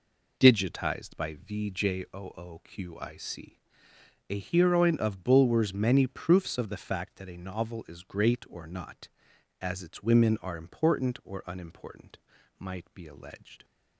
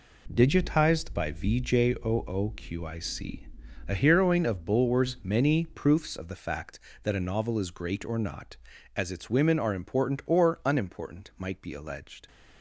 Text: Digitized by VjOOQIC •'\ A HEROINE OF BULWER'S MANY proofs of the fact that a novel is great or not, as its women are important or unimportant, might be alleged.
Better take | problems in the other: neither | none

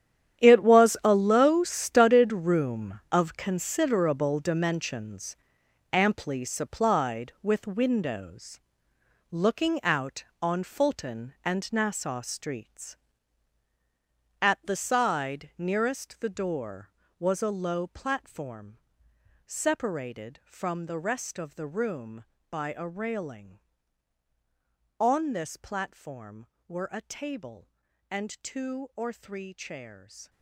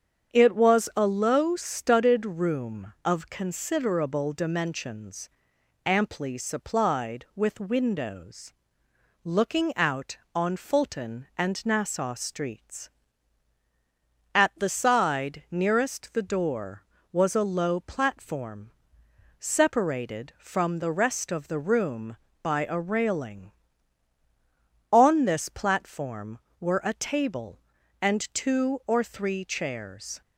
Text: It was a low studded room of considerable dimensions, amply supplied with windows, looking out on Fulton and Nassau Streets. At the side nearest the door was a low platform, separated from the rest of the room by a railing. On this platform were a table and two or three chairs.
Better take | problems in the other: second | gets quieter; strong; throughout; 14.5 dB // starts louder than the rest; strong; until 1.4 s; 10 dB; strong in the second

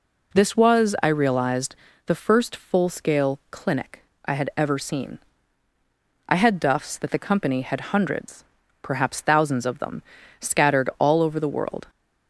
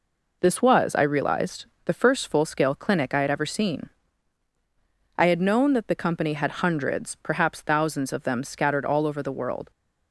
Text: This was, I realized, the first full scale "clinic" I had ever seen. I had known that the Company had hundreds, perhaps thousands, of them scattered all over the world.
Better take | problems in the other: second | pauses between "clinic" and "I"; slight; at 4.0 s; 0.20 s long // says "duffs" for "known"; at 6.6 s // pauses between "them" and "scattered"; slight; at 10.0 s; 0.36 s long

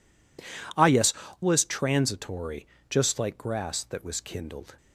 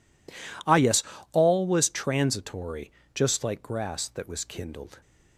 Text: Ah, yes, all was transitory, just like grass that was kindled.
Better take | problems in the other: second | skips "all"; at 1.2 s

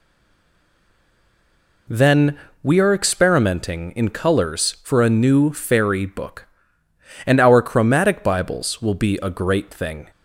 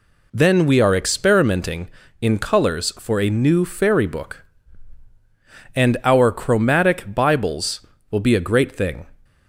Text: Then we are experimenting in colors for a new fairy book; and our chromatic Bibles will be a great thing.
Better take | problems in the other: second | stays silent before the first word; noticeable; until 1.8 s; 1.8 s long // pauses between "Then" and "we"; slight; at 2.3 s; 0.26 s long

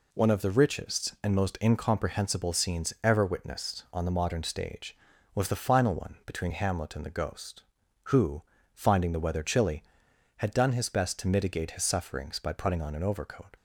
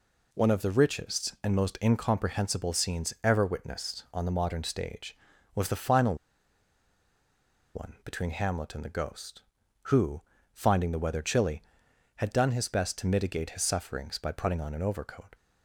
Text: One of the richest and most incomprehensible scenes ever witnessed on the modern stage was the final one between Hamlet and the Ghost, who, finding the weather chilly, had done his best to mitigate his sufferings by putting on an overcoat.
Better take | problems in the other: first | pauses between "final" and "one"; strong; at 6.1 s; 1.6 s long

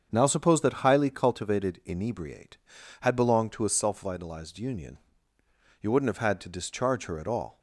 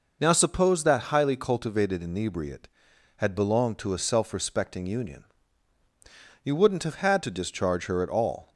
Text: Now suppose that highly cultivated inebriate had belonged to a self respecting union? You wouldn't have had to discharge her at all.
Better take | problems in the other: second | starts louder than the rest; strong; until 1.1 s; 7 dB // says "vitalized" for "respecting"; at 4.0 s

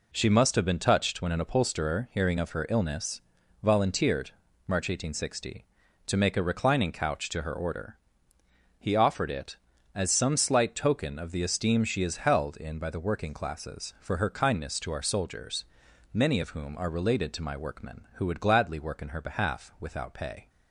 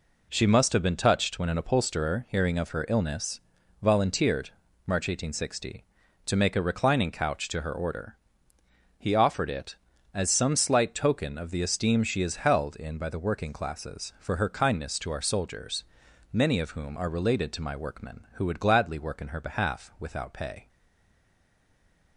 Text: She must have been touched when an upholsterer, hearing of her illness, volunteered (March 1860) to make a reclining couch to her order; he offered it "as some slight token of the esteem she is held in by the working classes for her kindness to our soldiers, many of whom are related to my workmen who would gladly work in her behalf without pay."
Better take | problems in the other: first | stays silent after the last word; noticeable; from 20.6 s on; 1.5 s long

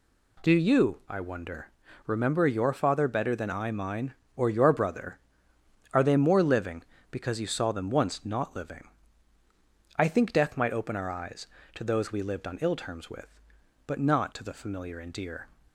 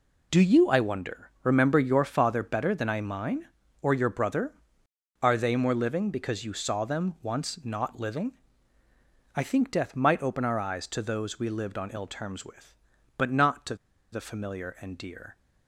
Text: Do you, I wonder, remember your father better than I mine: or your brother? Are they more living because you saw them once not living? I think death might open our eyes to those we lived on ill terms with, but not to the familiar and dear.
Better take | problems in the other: first | pauses between "to" and "the"; at 13.7 s; 0.36 s long

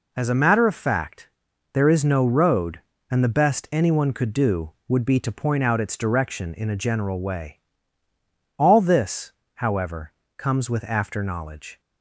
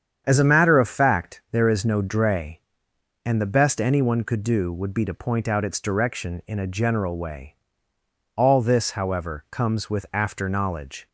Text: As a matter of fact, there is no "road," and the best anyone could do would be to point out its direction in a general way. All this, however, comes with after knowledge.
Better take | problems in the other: first | starts louder than the rest; strong; until 1.2 s; 8 dB // says "dray" for "road"; at 2.0 s

